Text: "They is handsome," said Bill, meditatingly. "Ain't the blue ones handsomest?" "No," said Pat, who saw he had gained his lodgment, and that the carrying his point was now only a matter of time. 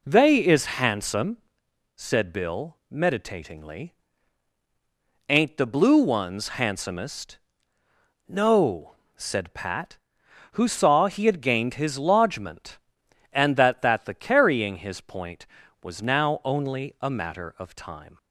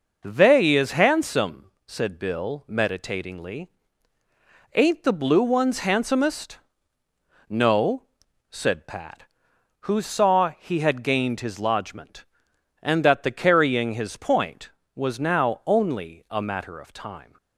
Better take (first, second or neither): second